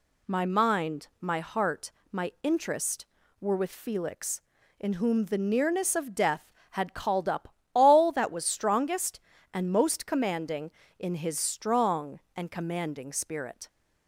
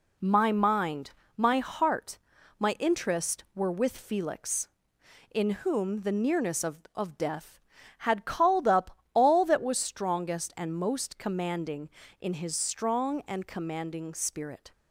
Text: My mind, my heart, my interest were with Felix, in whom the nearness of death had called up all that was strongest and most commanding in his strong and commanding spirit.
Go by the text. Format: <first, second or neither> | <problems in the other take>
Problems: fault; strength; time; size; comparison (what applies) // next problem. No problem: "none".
first | says "of" twice; at 6.9 s // pauses between "up" and "all"; slight; at 8.9 s; 0.16 s long; slight in the first